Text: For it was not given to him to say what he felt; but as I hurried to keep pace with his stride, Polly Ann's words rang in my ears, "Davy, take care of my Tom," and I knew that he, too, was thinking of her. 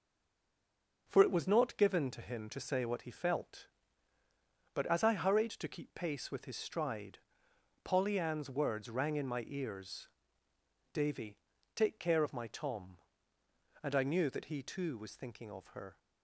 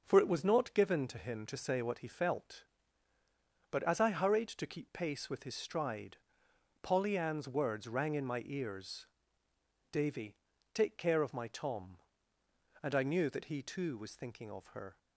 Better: second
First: stays silent before the first word; until 1.0 s; 1.0 s long // starts louder than the rest; until 2.0 s; 6.5 dB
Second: starts louder than the rest; until 1.0 s; 6.5 dB

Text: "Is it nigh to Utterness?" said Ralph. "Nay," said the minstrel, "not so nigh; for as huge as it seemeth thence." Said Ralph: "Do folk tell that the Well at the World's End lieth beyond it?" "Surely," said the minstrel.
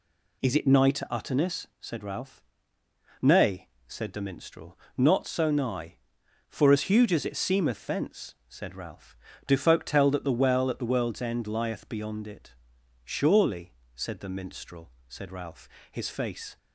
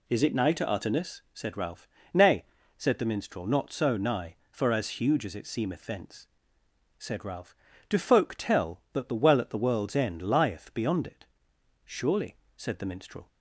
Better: second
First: goes on to say "Said Ralph his face"; from 15.0 s on; 1.5 s long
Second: none

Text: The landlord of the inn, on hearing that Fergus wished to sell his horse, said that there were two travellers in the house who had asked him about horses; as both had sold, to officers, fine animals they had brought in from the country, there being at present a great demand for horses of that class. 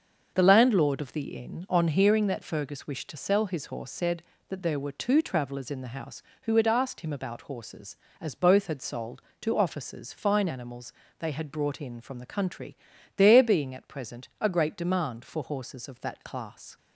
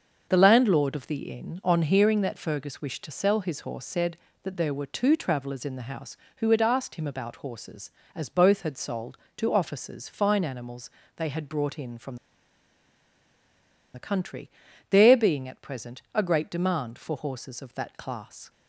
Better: first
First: starts louder than the rest; until 1.3 s; 6.5 dB // pauses between "animals" and "they"; slight; at 10.9 s; 0.26 s long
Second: starts louder than the rest; until 1.3 s; 6.5 dB // pauses between "animals" and "they"; slight; at 10.8 s; 0.26 s long // pauses between "from" and "the"; strong; at 12.1 s; 1.7 s long

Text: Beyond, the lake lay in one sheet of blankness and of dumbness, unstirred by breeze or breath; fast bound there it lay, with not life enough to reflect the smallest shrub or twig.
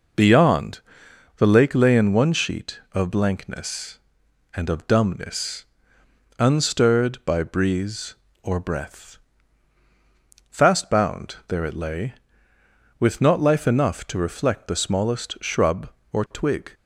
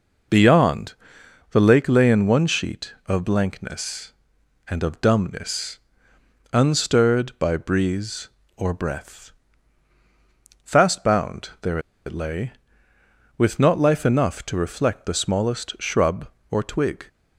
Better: first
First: none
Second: pauses between "there" and "it"; slight; at 11.7 s; 0.26 s long

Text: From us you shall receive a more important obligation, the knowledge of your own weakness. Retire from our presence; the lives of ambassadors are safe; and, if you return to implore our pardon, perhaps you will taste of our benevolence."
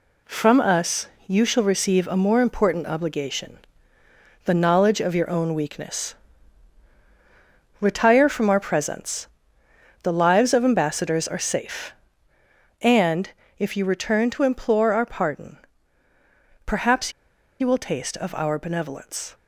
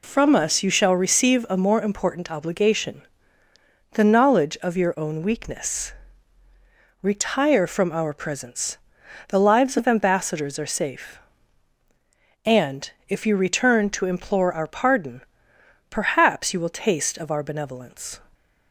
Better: second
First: pauses between "us" and "you"; slight; at 1.0 s; 0.20 s long // pauses between "perhaps" and "you"; noticeable; at 17.1 s; 0.48 s long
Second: none

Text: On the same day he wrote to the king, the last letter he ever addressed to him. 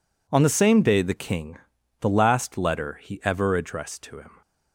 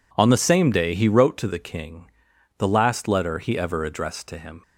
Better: second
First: skips "he wrote to"; at 1.0 s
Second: none

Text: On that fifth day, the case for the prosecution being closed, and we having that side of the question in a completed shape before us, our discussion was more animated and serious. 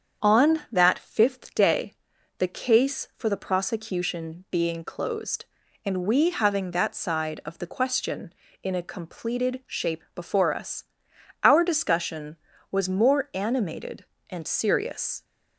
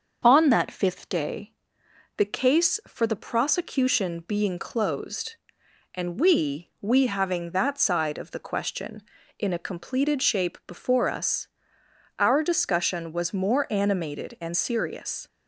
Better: first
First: starts louder than the rest; strong; until 1.3 s; 7.5 dB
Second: starts louder than the rest; until 1.2 s; 7 dB // says "we" twice; at 6.8 s

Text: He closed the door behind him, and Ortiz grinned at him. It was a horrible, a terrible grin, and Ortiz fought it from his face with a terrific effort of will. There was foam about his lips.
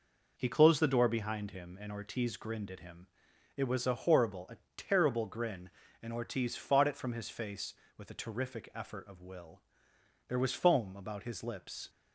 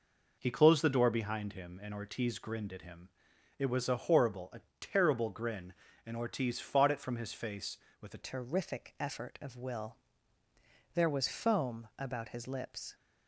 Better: first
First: pauses between "a" and "terrible"; slight; at 4.5 s; 0.18 s long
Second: pauses between "a" and "terrible"; slight; at 4.6 s; 0.18 s long // changes voice at "terrific"; from 8.2 s on; 4.7 s long

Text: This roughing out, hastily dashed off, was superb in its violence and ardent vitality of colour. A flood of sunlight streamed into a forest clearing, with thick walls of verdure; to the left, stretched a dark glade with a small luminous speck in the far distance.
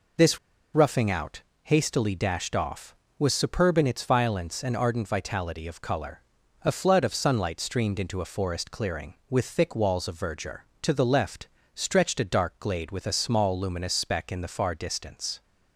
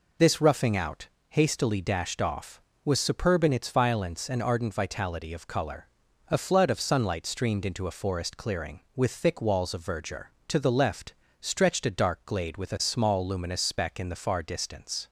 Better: second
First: pauses between "This" and "roughing"; slight; at 0.3 s; 0.35 s long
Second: none

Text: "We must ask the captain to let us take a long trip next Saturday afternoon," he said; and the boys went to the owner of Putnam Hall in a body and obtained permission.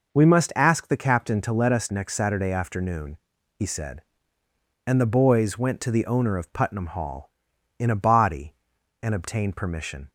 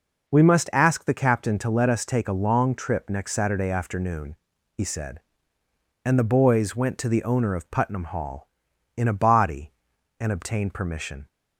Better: second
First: skips "take a long trip"; at 1.8 s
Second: none

